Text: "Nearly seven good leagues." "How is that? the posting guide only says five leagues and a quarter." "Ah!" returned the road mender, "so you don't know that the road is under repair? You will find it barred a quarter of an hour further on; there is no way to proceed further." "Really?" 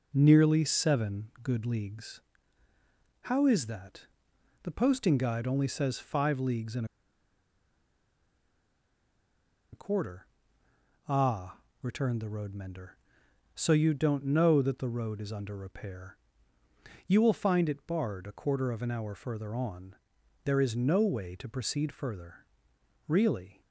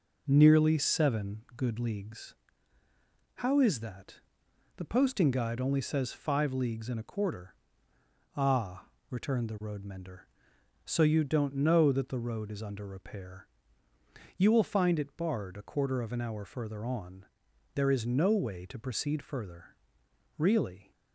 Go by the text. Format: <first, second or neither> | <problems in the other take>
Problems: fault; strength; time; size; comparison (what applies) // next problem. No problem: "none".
second | pauses between "and" and "a"; strong; at 6.8 s; 2.8 s long